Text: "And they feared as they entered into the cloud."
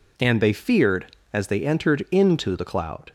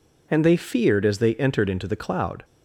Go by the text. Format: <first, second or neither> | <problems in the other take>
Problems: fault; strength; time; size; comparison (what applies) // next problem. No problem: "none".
neither | none